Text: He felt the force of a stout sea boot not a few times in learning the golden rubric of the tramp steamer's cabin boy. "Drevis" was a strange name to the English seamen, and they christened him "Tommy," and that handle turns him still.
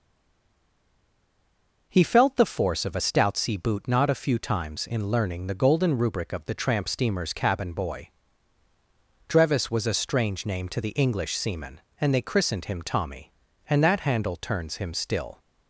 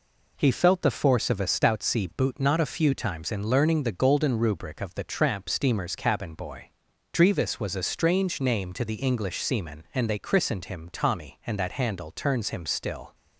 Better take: second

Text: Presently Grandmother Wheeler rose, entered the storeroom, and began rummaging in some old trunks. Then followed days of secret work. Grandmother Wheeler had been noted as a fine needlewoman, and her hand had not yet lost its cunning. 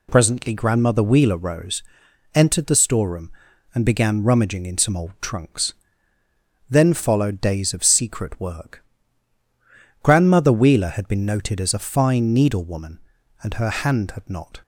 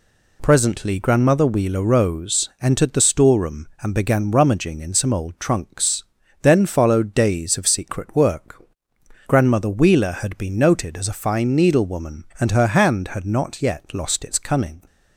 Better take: second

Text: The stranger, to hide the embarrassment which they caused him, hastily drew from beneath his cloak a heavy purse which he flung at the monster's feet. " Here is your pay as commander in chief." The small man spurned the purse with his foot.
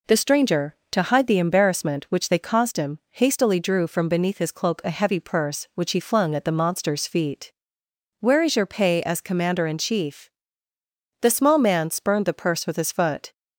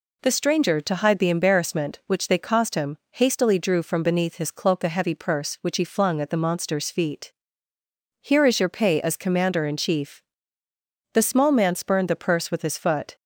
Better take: second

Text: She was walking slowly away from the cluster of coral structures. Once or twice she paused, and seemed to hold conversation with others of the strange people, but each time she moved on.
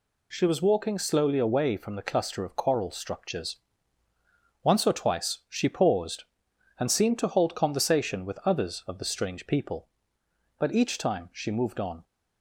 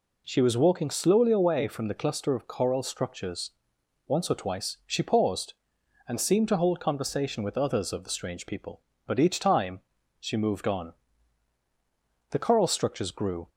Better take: first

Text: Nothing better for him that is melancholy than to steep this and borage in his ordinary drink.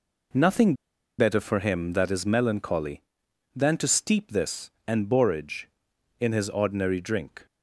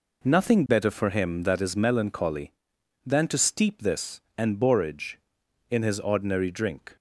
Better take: second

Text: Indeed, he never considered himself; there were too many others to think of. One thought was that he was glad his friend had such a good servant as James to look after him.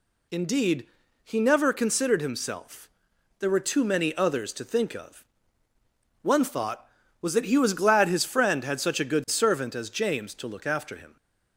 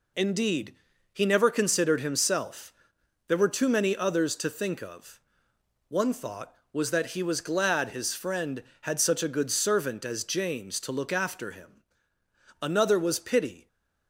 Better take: first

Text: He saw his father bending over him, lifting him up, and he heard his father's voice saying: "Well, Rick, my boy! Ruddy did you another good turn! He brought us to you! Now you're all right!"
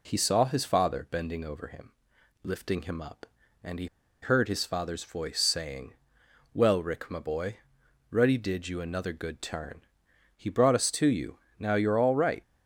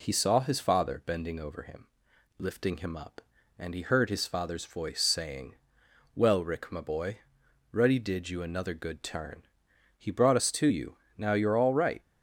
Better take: second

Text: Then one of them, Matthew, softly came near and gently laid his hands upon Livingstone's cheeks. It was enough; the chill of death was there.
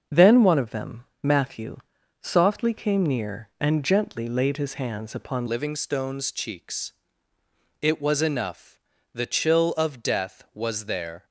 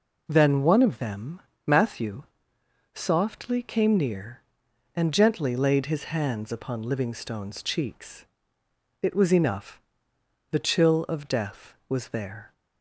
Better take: second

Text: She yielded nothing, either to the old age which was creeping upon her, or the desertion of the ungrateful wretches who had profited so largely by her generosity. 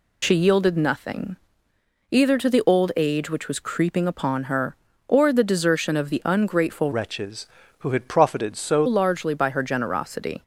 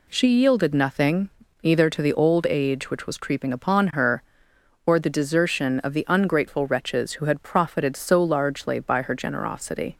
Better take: second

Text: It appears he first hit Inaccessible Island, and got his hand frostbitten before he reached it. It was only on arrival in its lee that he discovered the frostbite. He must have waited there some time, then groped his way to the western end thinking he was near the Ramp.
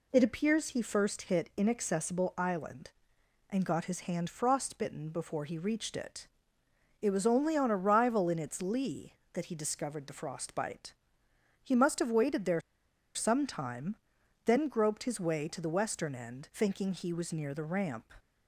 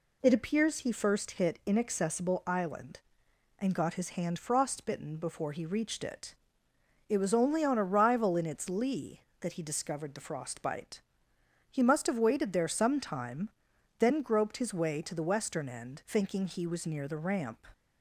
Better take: second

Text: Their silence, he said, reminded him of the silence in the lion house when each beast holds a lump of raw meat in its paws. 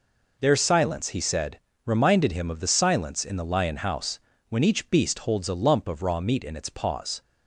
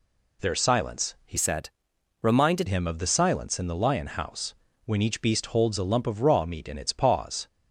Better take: first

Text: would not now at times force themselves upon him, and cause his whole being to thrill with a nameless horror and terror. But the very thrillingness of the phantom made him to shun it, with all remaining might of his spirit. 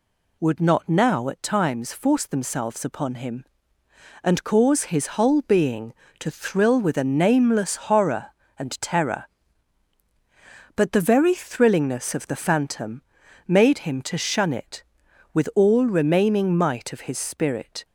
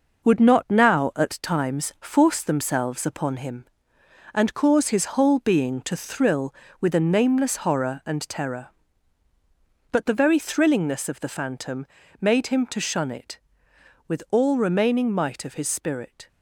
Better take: first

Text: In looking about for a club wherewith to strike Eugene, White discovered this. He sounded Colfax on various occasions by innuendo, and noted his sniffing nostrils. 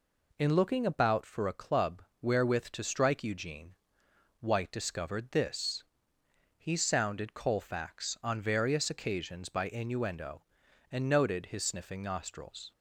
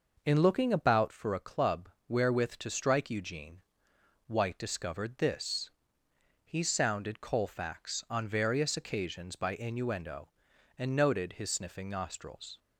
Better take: first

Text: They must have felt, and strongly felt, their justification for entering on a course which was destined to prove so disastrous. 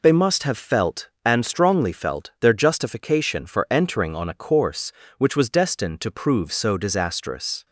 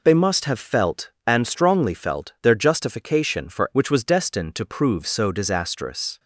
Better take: first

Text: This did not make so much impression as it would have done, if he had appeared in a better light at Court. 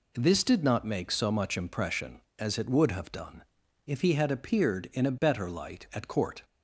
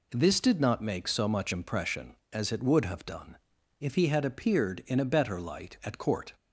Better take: neither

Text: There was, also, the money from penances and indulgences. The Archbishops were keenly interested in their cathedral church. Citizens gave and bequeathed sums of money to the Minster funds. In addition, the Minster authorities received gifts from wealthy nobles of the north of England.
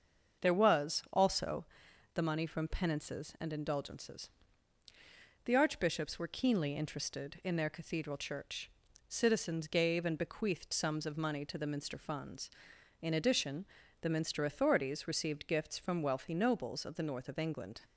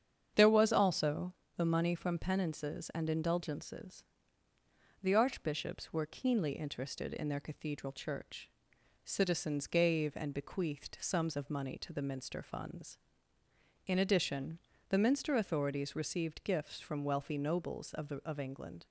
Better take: first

